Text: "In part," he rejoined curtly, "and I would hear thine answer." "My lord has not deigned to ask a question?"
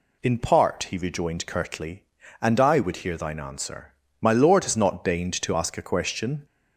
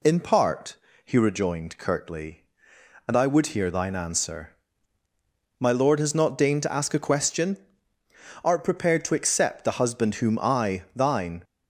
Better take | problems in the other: first | goes on to say "Art prepared to accept the husband whom I thine"; strong; from 8.4 s on; 3.0 s long

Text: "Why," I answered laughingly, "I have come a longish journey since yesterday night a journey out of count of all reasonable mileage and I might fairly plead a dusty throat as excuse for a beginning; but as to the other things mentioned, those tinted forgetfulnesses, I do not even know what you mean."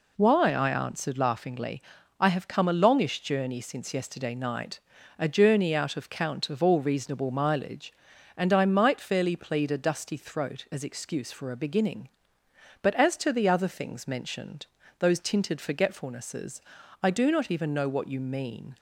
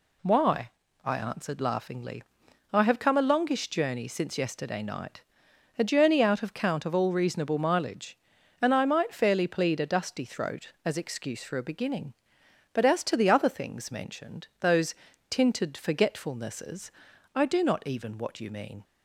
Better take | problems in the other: first | pauses between "night" and "a"; noticeable; at 5.2 s; 0.56 s long; also in the first // pauses between "those" and "tinted"; slight; at 14.9 s; 0.36 s long // skips "know"; at 18.1 s

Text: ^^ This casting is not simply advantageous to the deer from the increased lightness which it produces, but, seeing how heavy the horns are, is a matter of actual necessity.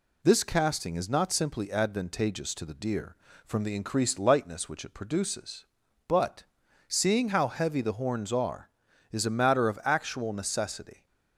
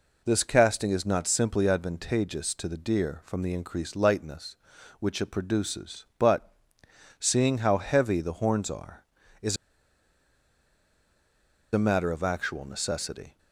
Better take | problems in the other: first | pauses between "is" and "a"; strong; at 9.5 s; 2.1 s long

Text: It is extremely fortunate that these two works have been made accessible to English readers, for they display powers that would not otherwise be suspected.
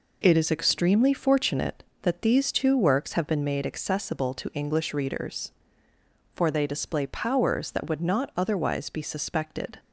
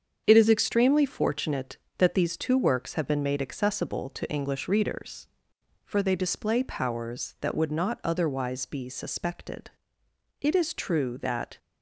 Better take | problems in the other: first | starts louder than the rest; strong; until 1.2 s; 7.5 dB // goes on to say "It is true that"; noticeable; from 10.4 s on; 1.1 s long

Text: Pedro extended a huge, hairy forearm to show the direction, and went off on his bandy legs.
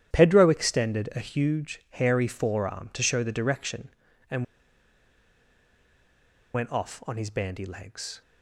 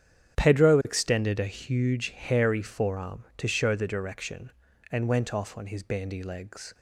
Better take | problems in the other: second | starts louder than the rest; strong; until 1.2 s; 10.5 dB; strong in the second // pauses between "and" and "went"; strong; at 4.4 s; 2.1 s long

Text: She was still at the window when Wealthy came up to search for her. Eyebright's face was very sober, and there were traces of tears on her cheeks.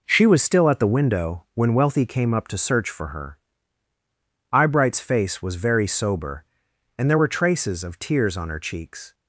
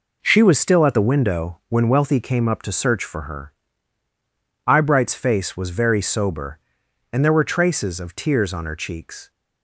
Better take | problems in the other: neither | none

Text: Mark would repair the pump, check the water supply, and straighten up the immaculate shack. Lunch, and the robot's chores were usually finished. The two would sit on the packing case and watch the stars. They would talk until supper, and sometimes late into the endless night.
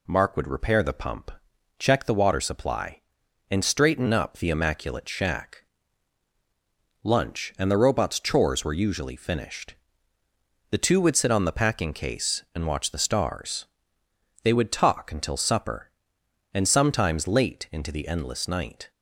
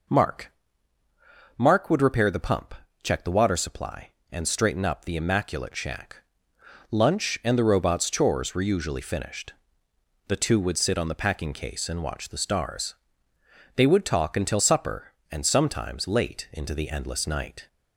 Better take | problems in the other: first | says "Mark" twice; at 1.5 s

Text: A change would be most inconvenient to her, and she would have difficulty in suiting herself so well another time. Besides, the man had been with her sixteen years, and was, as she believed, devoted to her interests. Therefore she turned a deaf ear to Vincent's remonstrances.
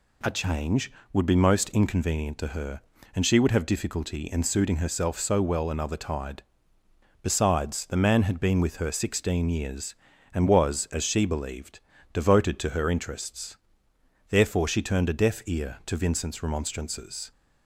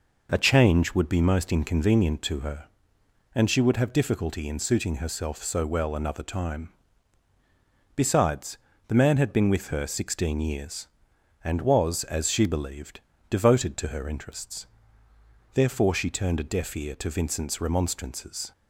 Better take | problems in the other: second | says "tide" for "time"; at 5.9 s

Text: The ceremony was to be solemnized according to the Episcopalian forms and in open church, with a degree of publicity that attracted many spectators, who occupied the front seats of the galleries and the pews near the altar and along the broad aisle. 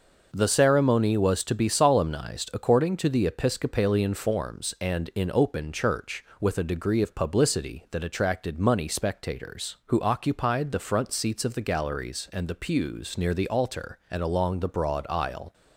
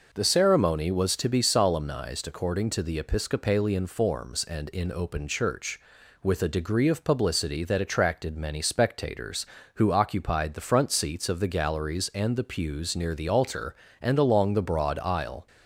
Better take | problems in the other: second | says "money" for "many"; at 8.5 s

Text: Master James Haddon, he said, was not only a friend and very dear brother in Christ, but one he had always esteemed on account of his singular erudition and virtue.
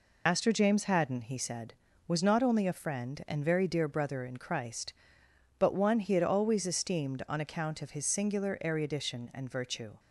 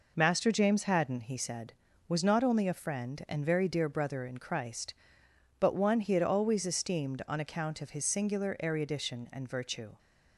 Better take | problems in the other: second | loses the start of "Master"; at 0.2 s; 90 ms

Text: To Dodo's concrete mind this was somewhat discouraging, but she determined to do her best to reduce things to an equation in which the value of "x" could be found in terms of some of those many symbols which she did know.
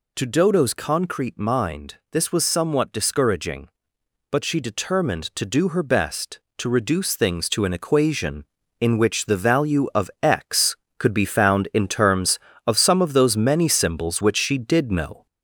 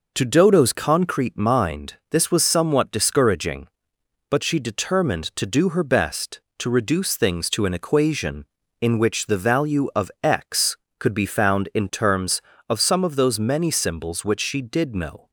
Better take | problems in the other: second | gets louder; throughout; 4 dB // pauses between "mind" and "this"; slight; at 1.9 s; 0.16 s long; slight in the second

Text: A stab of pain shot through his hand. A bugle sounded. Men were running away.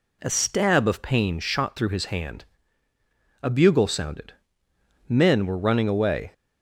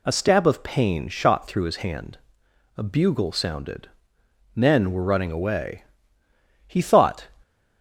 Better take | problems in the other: first | goes on to say "He thought"; from 6.6 s on; 0.60 s long

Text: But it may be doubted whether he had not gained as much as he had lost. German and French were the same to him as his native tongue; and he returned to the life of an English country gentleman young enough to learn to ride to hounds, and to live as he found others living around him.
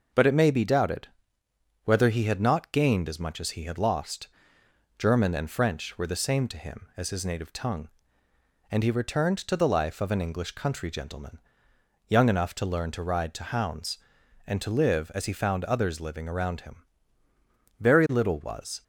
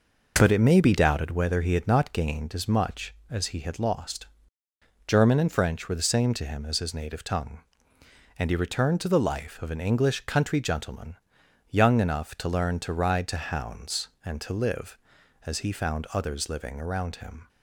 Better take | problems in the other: second | pauses between "doubted" and "whether"; noticeable; at 1.0 s; 0.76 s long // pauses between "gentleman" and "young"; noticeable; at 11.3 s; 0.70 s long; noticeable in the second // goes on to say "Very little was"; noticeable; from 17.7 s on; 1.0 s long

